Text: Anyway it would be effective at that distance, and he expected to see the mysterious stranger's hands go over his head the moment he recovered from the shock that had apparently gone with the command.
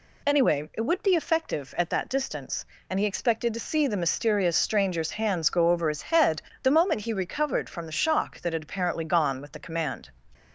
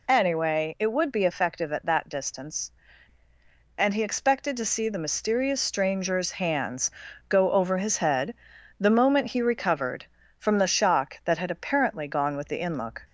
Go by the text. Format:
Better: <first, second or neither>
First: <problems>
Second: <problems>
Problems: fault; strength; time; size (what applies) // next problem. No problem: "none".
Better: first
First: pauses between "head" and "the"; slight; at 6.4 s; 0.22 s long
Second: pauses between "hands" and "go"; at 6.8 s; 0.40 s long // pauses between "head" and "the"; at 8.3 s; 0.44 s long // says "inlook" for "command"; at 12.5 s